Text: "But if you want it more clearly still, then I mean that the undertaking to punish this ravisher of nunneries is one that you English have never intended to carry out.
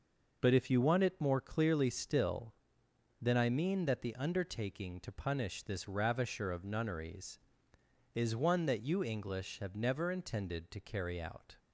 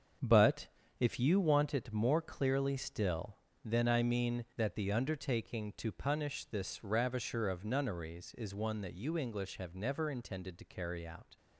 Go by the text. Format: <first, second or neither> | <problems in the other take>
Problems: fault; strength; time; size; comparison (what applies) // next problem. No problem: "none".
first | gets quieter; strong; throughout; 9 dB // pauses between "But" and "if"; slight; at 0.6 s; 0.32 s long